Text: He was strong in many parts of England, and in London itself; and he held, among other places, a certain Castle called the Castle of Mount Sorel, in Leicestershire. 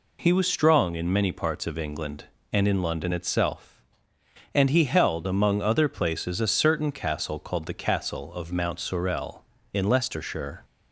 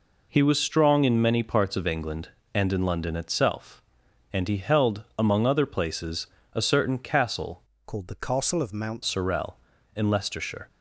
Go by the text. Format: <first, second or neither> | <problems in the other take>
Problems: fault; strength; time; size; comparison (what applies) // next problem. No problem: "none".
first | changes voice from "called" to "Mount"; from 7.8 to 9.0 s; 1.2 s long